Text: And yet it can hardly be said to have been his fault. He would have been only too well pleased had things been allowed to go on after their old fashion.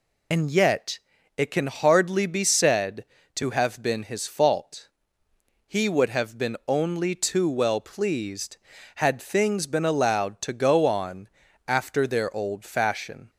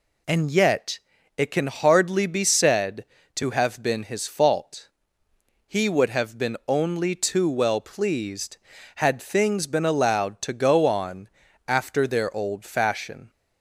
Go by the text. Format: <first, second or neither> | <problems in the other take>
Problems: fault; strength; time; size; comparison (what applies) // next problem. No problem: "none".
second | loses the start of "And"; at 0.3 s; 50 ms // pauses between "yet" and "it"; slight; at 0.9 s; 0.36 s long; slight in the second // pauses between "on" and "after"; at 11.2 s; 0.38 s long; also in the second